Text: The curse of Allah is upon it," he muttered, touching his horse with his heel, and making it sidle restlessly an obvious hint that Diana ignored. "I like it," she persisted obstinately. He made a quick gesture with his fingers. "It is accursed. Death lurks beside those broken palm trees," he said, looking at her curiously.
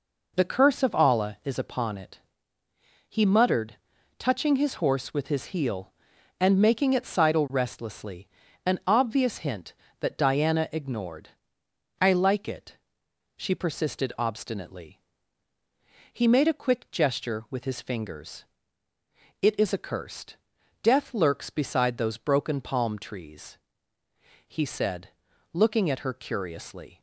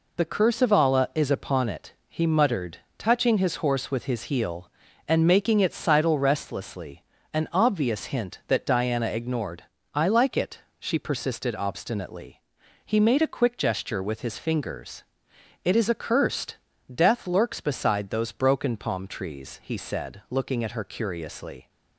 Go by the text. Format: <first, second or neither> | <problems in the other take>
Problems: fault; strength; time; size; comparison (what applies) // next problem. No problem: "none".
neither | pauses between "restlessly" and "an"; the same in both